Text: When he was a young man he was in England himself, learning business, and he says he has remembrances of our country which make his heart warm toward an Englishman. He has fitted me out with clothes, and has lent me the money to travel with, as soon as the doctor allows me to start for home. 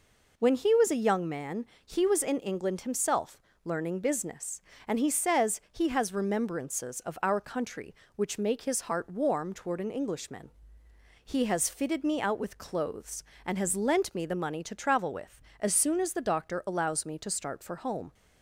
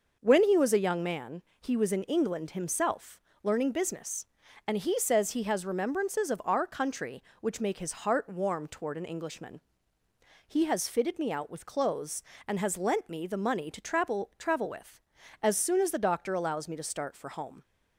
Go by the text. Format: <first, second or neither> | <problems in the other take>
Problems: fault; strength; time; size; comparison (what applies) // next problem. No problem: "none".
first | pauses between "man" and "he"; slight; at 1.4 s; 0.18 s long; slight in the first // says "travel" twice; at 14.3 s